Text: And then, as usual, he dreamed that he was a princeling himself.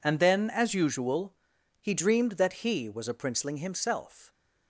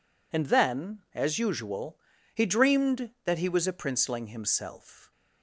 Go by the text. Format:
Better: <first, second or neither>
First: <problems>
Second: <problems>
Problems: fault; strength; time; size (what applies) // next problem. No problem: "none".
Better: neither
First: none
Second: none